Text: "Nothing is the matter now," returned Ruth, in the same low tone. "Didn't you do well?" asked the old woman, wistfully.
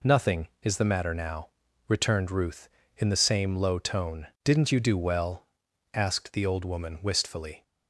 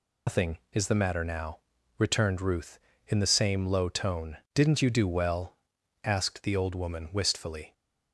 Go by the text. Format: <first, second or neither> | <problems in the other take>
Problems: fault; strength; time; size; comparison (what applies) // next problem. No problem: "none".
first | loses the start of "Nothing"; at 0.2 s; 150 ms